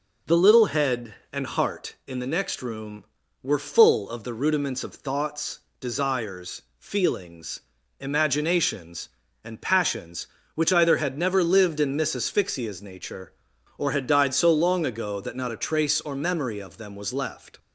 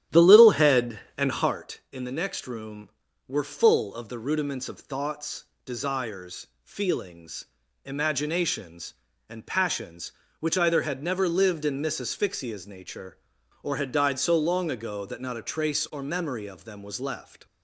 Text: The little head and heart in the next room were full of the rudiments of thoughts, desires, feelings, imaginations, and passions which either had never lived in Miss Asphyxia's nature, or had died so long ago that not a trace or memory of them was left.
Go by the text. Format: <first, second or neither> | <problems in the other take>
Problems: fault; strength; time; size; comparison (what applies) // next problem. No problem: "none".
first | starts louder than the rest; strong; until 1.5 s; 11.5 dB